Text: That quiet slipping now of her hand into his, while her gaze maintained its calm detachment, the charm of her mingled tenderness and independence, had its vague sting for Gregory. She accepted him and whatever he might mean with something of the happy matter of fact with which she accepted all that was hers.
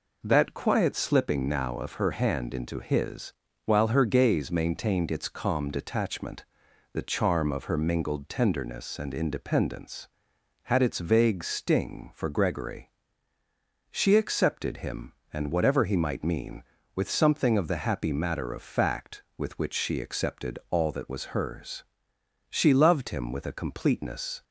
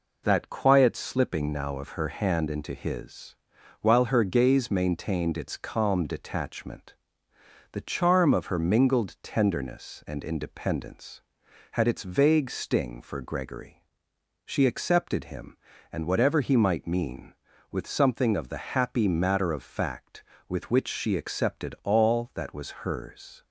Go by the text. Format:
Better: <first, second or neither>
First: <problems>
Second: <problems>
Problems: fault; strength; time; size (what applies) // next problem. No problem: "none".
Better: second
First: goes on to say "She loved him with a completeness"; strong; from 22.4 s on; 1.9 s long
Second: none